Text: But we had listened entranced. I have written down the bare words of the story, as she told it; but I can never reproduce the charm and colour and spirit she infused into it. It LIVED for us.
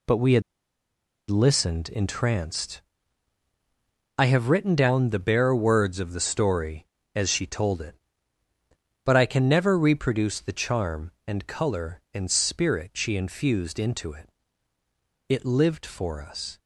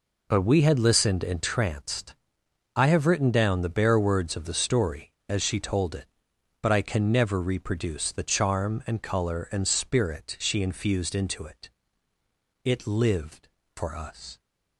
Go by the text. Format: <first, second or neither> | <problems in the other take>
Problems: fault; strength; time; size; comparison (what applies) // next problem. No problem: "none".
second | pauses between "had" and "listened"; noticeable; at 0.4 s; 0.88 s long